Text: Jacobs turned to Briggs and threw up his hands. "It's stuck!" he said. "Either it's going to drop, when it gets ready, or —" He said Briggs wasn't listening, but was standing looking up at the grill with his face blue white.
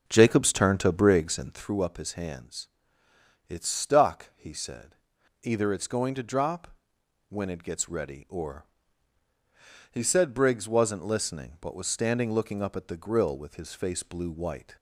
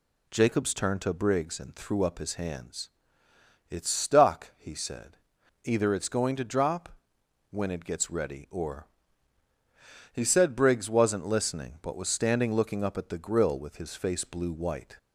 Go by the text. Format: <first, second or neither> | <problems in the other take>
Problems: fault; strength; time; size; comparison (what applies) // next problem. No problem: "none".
second | starts louder than the rest; noticeable; until 1.6 s; 5.5 dB